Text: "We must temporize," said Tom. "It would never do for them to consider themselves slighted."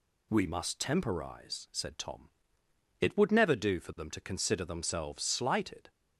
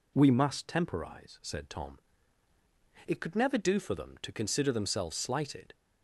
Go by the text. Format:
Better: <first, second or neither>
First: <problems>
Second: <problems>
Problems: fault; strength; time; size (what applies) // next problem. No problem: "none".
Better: first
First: none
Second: says "could" for "would"; at 3.2 s